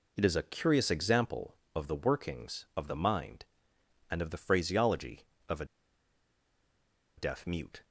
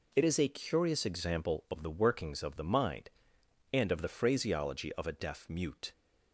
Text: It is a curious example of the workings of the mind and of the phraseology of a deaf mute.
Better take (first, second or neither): second